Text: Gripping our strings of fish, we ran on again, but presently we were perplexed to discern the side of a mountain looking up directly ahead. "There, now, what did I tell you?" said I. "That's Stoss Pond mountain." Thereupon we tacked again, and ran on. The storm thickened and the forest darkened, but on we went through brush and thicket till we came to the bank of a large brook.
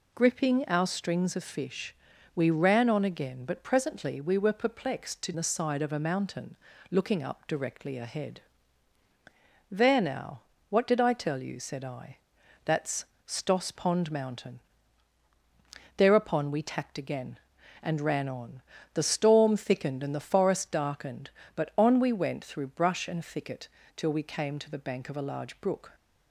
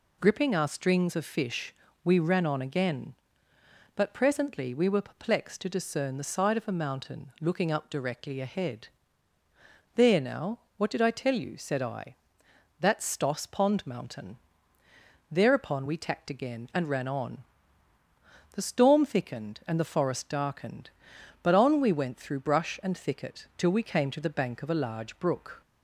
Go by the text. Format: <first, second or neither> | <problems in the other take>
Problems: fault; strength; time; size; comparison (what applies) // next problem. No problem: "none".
second | skips "discern"; at 5.3 s // pauses between "mountain" and "looking"; slight; at 6.5 s; 0.32 s long // pauses between "That's" and "Stoss"; slight; at 13.0 s; 0.20 s long // pauses between "thicket" and "till"; slight; at 23.6 s; 0.26 s long